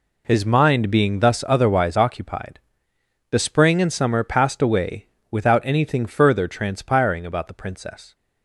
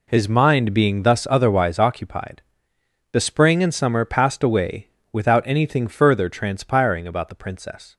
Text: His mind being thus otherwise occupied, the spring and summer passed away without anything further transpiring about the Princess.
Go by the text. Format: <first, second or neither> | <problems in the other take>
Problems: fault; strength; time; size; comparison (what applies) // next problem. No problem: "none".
neither | pauses between "away" and "without"; slight; the same in both